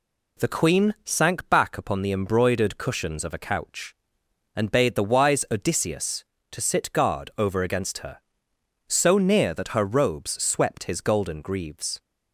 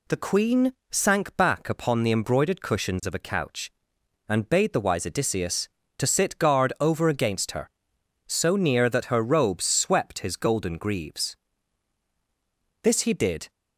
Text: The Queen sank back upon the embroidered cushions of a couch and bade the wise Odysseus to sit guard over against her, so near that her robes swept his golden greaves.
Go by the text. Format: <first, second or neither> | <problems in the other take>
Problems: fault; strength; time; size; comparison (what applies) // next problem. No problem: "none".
first | pauses between "Queen" and "sank"; slight; at 0.7 s; 0.16 s long // goes on to say "This he did"; noticeable; from 12.8 s on; 0.68 s long